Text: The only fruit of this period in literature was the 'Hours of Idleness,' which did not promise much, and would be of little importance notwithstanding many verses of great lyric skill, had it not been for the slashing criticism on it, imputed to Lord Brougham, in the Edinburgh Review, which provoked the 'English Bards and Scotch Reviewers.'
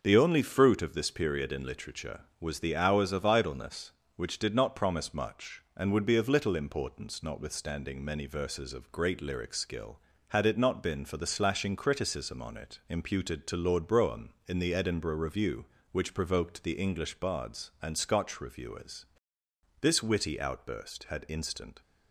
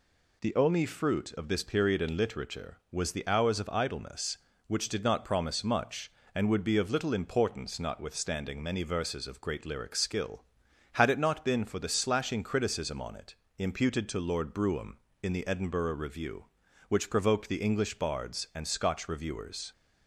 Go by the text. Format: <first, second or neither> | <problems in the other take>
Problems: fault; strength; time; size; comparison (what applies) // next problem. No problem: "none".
second | starts louder than the rest; noticeable; until 1.0 s; 6 dB // goes on to say "This witty outburst had instant"; strong; from 19.8 s on; 2.0 s long